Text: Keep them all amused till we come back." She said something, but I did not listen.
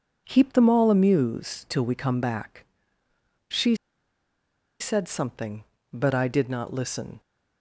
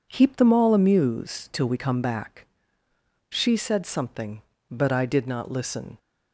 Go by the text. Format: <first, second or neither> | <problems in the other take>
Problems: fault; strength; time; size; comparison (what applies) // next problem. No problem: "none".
second | pauses between "She" and "said"; at 3.7 s; 1.0 s long